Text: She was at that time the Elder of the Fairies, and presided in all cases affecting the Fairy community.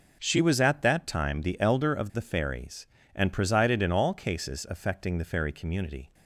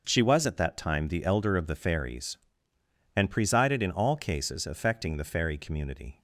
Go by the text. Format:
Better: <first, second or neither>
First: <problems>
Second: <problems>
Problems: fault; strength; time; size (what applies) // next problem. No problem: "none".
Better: neither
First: none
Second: none